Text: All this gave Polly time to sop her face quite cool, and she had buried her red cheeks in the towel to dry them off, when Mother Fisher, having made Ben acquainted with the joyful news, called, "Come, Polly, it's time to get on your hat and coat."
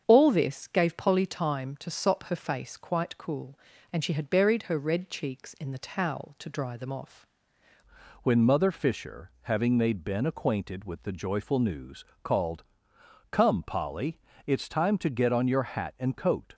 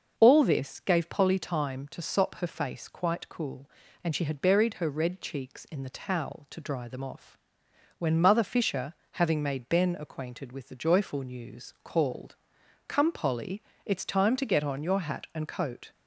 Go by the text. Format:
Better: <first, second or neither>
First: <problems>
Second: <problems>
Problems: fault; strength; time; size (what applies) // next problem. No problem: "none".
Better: second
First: starts louder than the rest; strong; until 1.0 s; 7.5 dB // changes voice at "when"; from 8.2 s on; 8.3 s long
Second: starts louder than the rest; noticeable; until 1.1 s; 6 dB